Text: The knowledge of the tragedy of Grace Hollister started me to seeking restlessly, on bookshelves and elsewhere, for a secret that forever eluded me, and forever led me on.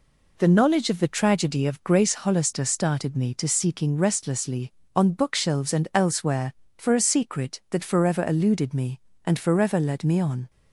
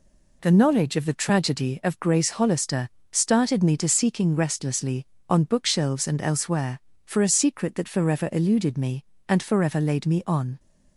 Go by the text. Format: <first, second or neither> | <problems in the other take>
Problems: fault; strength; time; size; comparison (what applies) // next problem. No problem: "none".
first | pauses between "Hollister" and "started"; slight; at 2.8 s; 0.24 s long // says "laid" for "led"; at 9.8 s